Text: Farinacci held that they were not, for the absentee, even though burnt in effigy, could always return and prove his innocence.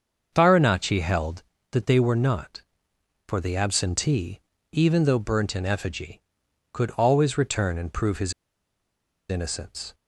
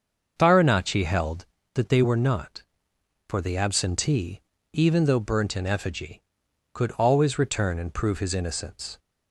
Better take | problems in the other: second | starts louder than the rest; until 1.3 s; 6.5 dB; also in the second // pauses between "his" and "innocence"; noticeable; at 8.3 s; 0.97 s long

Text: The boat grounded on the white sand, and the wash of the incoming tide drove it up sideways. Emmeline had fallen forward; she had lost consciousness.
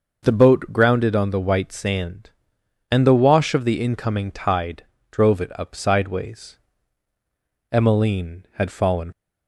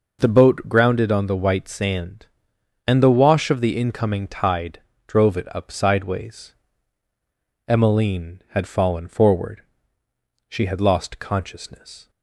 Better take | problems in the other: second | pauses between "tide" and "drove"; slight; at 4.8 s; 0.26 s long; slight in the second // stops before "forward she had lost consciousness"; at 9.1 s

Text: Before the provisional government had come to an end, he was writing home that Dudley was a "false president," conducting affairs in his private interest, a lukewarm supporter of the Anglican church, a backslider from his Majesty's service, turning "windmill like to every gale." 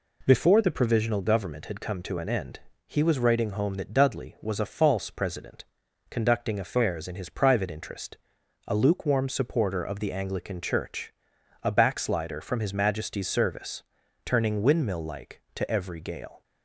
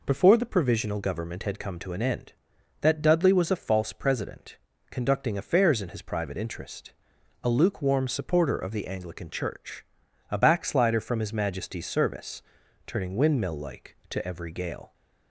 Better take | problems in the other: first | skips "he was writing home"; at 2.5 s

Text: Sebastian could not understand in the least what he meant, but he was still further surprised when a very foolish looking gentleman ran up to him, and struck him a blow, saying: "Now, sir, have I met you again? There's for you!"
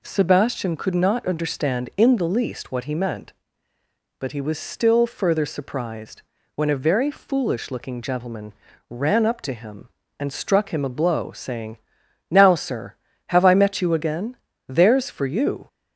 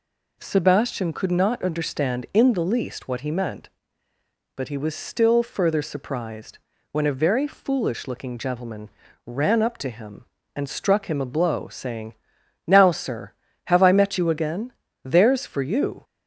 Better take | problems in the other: neither | pauses between "surprised" and "when"; slight; the same in both // pauses between "gentleman" and "ran"; slight; the same in both

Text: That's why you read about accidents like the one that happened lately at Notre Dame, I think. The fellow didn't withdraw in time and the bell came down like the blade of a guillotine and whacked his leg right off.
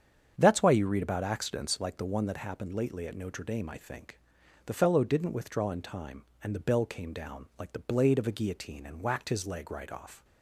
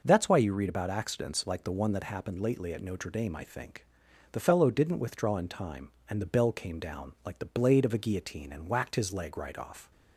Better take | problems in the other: second | starts louder than the rest; strong; until 1.9 s; 7.5 dB

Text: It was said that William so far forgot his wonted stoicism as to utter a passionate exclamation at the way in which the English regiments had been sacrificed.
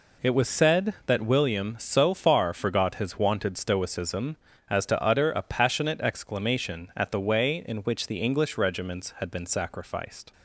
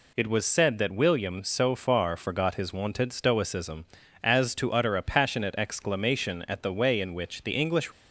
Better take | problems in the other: first | stops before "regiments had been sacrificed"; at 7.9 s

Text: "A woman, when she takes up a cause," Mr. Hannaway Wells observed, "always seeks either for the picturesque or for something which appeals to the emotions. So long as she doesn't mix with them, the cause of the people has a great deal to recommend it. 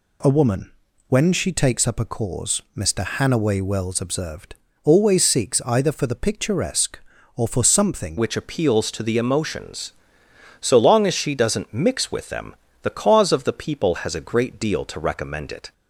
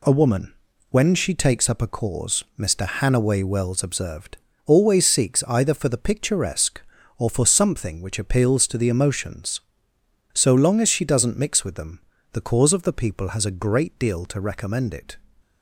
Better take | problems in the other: second | changes voice at "which"; from 8.1 s on; 7.6 s long

